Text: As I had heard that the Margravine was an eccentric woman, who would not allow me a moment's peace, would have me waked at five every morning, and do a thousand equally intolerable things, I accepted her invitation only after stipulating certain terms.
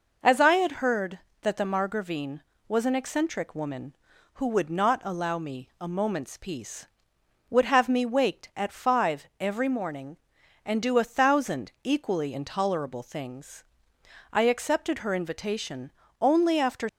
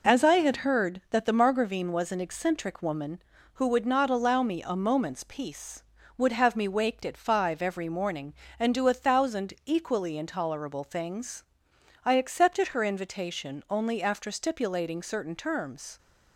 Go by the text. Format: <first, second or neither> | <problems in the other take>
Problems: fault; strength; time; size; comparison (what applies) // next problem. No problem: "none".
second | pauses between "invitation" and "only"; slight; at 15.9 s; 0.30 s long // stops before "stipulating certain terms"; at 16.8 s